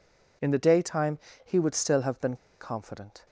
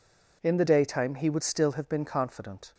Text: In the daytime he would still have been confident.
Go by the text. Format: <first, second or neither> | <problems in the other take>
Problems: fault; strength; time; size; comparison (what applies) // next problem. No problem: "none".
second | pauses between "daytime" and "he"; slight; at 1.1 s; 0.26 s long // pauses between "been" and "confident"; slight; at 2.3 s; 0.25 s long